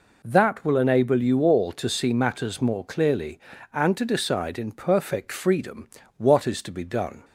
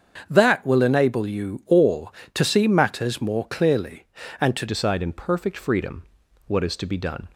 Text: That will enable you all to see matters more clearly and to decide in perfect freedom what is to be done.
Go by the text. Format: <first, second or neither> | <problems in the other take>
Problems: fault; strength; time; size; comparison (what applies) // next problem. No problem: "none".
first | starts louder than the rest; until 1.2 s; 7 dB // changes voice at "decide"; from 4.6 s on; 2.6 s long // pauses between "freedom" and "what"; at 6.0 s; 0.42 s long; slight in the first